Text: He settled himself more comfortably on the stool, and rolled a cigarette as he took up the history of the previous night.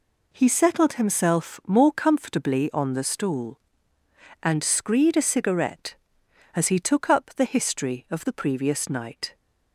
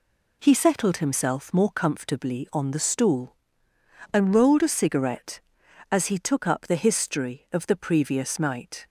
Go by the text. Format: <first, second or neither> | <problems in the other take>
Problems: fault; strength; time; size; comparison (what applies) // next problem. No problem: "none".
second | says "screed" for "rolled"; at 4.6 s